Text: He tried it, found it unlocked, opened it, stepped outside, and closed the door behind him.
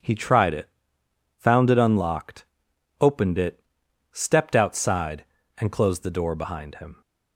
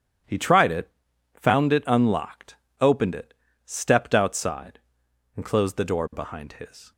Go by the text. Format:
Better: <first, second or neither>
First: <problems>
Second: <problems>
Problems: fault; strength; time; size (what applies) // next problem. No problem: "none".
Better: first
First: none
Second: starts louder than the rest; strong; until 1.6 s; 9.5 dB // says "his" for "him"; at 6.5 s